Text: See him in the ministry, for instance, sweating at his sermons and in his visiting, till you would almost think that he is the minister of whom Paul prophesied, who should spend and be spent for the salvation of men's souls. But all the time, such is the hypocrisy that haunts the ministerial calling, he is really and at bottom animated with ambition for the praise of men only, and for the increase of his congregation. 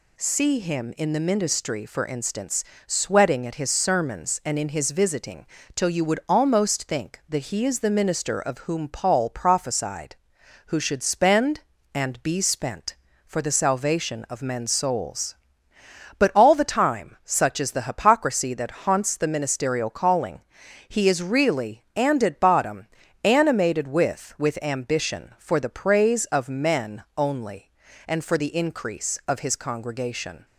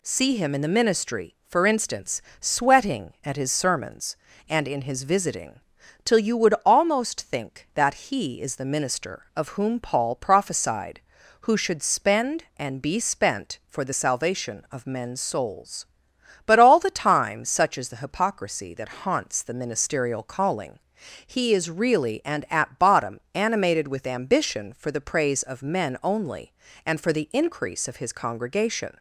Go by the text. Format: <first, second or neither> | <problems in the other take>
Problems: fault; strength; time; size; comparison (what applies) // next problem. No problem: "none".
second | pauses between "bottom" and "animated"; slight; at 22.8 s; 0.36 s long // says "with" twice; at 24.3 s // pauses between "men" and "only"; slight; at 27.0 s; 0.16 s long